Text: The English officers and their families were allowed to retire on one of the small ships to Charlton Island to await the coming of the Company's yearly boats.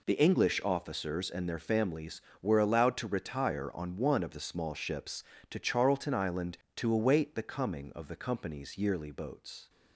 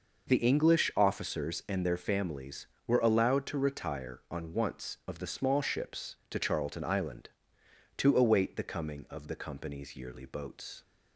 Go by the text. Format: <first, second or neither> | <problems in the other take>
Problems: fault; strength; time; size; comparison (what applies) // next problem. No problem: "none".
first | says "once" for "one"; at 4.5 s